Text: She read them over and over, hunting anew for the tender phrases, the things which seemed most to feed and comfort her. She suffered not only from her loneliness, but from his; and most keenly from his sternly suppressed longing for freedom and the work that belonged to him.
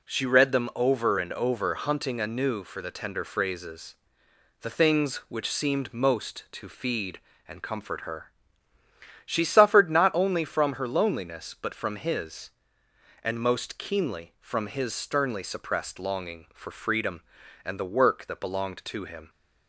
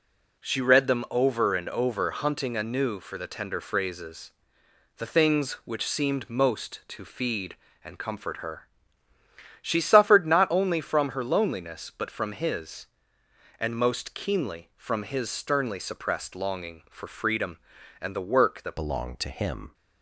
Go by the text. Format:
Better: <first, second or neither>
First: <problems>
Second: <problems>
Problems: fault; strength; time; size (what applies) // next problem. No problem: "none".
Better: first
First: none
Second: changes voice at "belonged"; from 18.7 s on; 1.0 s long